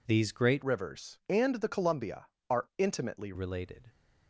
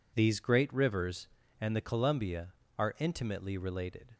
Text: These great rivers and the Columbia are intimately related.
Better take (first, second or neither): second